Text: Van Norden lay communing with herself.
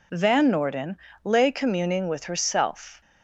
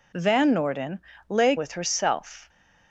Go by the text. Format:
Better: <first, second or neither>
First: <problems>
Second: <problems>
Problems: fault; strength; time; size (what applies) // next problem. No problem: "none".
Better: first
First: pauses between "Norden" and "lay"; slight; at 0.9 s; 0.28 s long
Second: pauses between "Norden" and "lay"; slight; at 0.9 s; 0.30 s long // skips "communing"; at 1.5 s